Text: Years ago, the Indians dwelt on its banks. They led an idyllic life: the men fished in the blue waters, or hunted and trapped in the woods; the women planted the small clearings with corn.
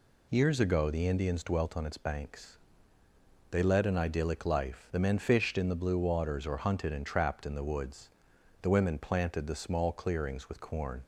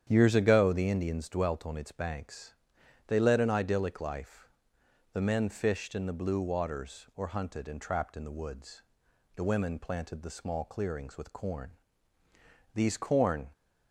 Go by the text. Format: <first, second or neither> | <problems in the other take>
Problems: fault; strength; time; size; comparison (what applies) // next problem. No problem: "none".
first | starts louder than the rest; strong; until 1.1 s; 9 dB // goes on to say "These corn"; noticeable; from 12.7 s on; 0.78 s long